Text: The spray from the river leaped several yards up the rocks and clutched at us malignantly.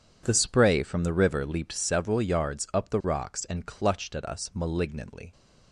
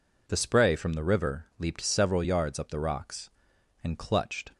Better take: first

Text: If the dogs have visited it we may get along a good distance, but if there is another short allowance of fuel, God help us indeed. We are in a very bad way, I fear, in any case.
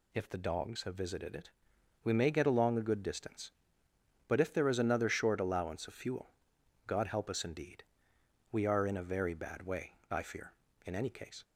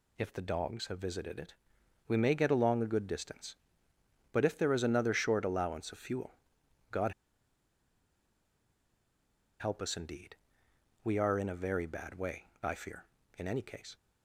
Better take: first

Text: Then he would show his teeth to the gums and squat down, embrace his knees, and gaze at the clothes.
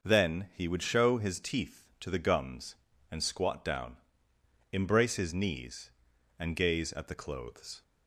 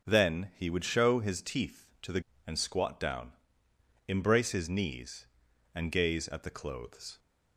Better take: first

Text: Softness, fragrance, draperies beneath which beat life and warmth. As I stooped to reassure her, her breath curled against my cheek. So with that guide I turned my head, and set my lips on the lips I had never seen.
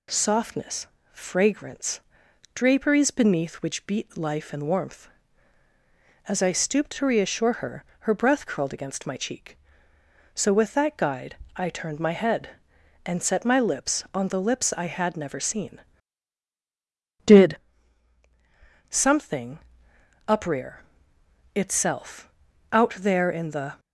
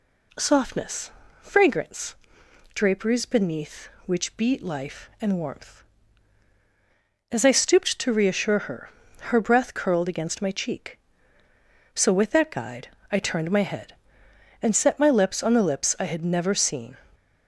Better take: second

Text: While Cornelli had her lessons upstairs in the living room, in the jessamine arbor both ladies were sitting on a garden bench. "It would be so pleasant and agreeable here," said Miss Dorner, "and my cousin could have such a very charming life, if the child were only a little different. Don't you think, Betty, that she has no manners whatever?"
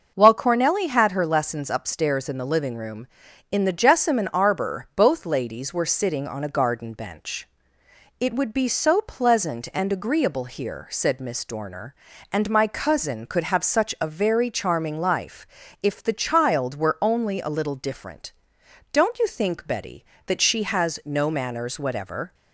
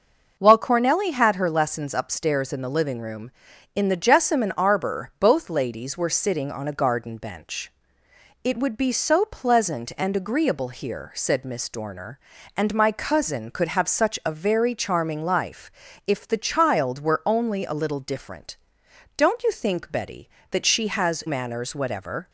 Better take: first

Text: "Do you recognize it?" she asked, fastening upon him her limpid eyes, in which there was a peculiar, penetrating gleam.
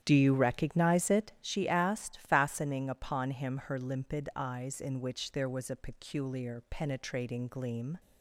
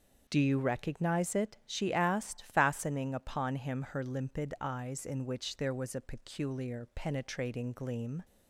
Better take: second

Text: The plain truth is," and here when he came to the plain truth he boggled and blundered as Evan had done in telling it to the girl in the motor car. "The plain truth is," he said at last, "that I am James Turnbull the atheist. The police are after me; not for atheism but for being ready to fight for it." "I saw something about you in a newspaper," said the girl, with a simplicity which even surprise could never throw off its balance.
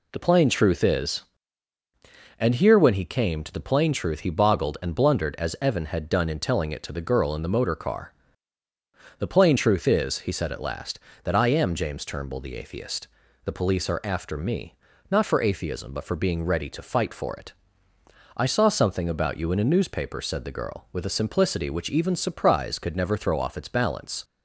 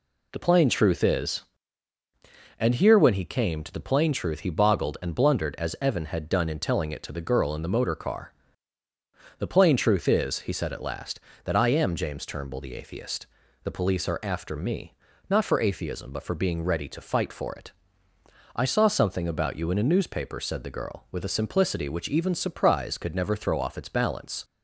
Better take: neither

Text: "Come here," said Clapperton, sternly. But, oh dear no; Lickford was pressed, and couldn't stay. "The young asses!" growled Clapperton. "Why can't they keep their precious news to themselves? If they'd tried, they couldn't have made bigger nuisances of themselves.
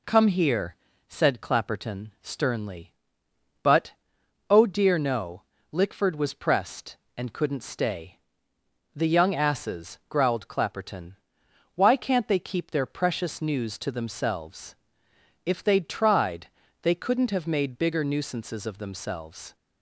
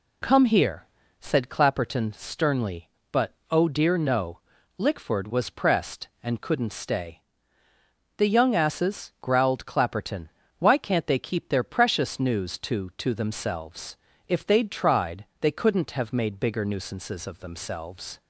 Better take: first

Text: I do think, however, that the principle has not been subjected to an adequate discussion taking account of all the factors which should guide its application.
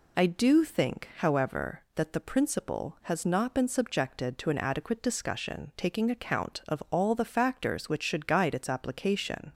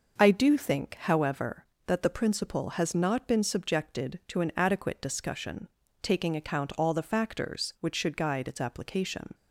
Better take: first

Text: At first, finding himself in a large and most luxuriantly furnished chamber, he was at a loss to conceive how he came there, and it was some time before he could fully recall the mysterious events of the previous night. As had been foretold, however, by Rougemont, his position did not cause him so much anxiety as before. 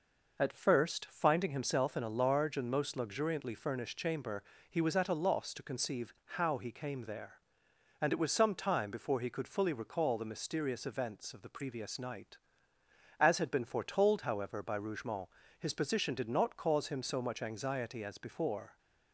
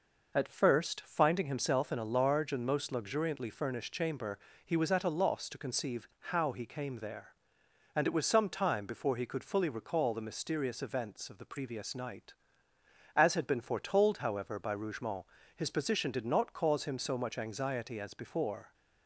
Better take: neither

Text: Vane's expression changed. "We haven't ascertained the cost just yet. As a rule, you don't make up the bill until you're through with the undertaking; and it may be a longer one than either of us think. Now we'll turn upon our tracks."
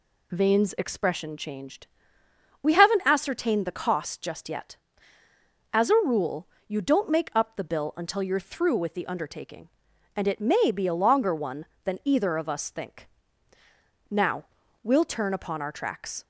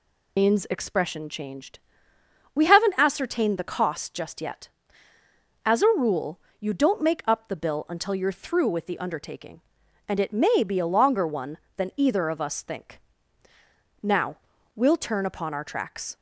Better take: first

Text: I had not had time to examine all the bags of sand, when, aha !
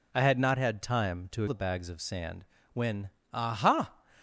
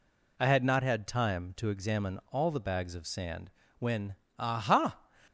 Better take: second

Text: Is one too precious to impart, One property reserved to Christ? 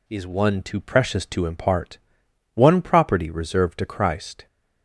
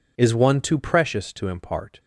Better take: first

